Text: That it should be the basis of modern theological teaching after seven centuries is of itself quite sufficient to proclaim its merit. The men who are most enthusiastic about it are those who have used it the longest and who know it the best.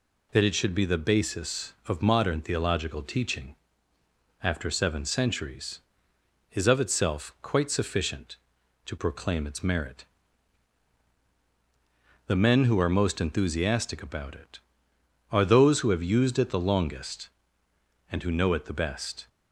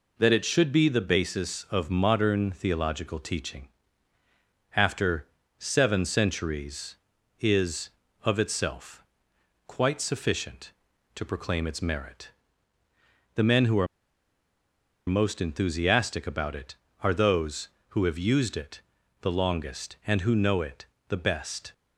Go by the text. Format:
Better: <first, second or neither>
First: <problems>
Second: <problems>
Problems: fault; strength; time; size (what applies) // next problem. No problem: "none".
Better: first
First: pauses between "teaching" and "after"; noticeable; at 3.5 s; 0.88 s long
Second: pauses between "teaching" and "after"; at 3.6 s; 1.1 s long // pauses between "after" and "seven"; slight; at 5.2 s; 0.32 s long // pauses between "itself" and "quite"; noticeable; at 9.0 s; 0.64 s long // pauses between "are" and "most"; at 13.8 s; 1.2 s long // pauses between "it" and "the"; at 18.8 s; 0.40 s long // pauses between "it" and "the"; slight; at 20.8 s; 0.24 s long